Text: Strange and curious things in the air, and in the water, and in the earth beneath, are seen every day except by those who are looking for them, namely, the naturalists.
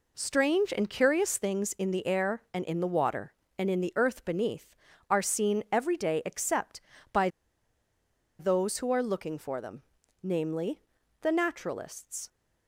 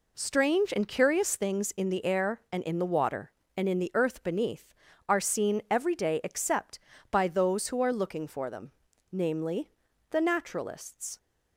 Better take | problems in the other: second | pauses between "by" and "those"; at 7.2 s; 1.1 s long

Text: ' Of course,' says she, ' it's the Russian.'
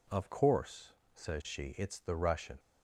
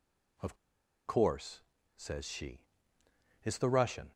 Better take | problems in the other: first | pauses between "Of" and "course"; noticeable; at 0.5 s; 0.53 s long

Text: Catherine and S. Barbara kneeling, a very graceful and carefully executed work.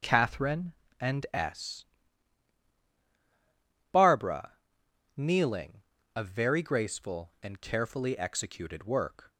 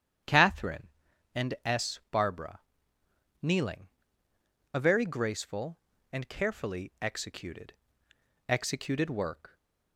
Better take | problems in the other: first | starts louder than the rest; strong; until 1.8 s; 9.5 dB // pauses between "Barbara" and "kneeling"; noticeable; at 2.6 s; 0.80 s long; noticeable in the first // says "executed" twice; at 8.4 s

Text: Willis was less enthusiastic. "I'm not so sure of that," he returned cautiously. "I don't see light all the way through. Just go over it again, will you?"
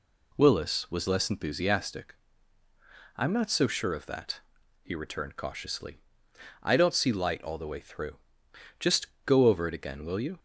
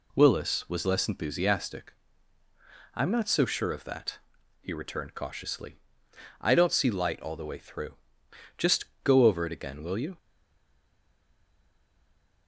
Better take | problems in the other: first | pauses between "Just" and "go"; slight; at 8.8 s; 0.20 s long; slight in the first // stays silent after the last word; from 10.1 s on; 2.3 s long

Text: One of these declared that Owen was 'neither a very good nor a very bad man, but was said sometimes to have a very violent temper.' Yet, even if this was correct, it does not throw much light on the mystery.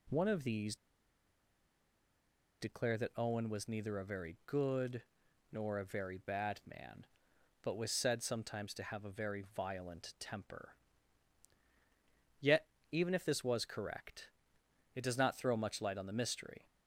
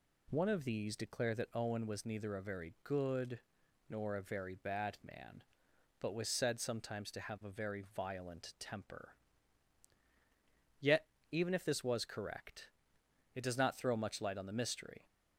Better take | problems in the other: second | pauses between "these" and "declared"; strong; at 0.7 s; 1.8 s long // pauses between "good" and "nor"; noticeable; at 5.0 s; 0.50 s long; noticeable in the second

